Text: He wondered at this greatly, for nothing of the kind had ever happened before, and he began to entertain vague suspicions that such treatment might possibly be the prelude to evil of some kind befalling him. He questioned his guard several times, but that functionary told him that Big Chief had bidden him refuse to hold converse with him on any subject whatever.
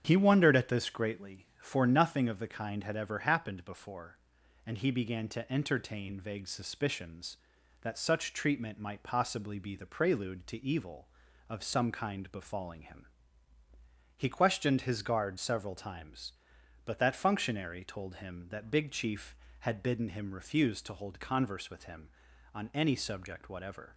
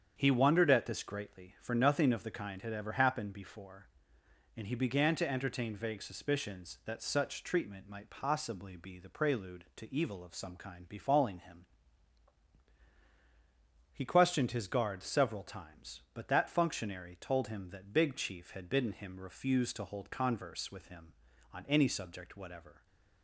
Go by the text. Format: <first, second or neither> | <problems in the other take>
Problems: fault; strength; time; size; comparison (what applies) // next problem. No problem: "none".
neither | starts louder than the rest; strong; the same in both